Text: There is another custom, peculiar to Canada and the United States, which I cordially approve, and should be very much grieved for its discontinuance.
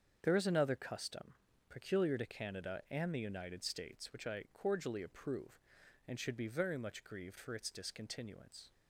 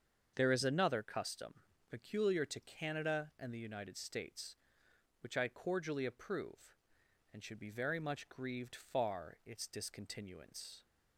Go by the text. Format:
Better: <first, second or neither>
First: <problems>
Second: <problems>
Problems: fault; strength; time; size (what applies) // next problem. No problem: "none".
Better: first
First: starts louder than the rest; strong; until 1.2 s; 7.5 dB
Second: starts louder than the rest; until 1.3 s; 7 dB // says "far" for "for"; at 8.7 s